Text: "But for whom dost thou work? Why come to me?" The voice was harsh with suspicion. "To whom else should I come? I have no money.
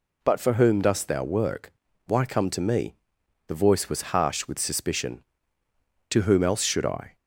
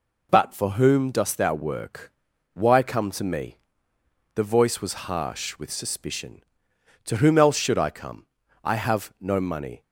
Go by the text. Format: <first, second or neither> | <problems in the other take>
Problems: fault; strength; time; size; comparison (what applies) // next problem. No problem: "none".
second | stops before "come I have no money"; at 7.1 s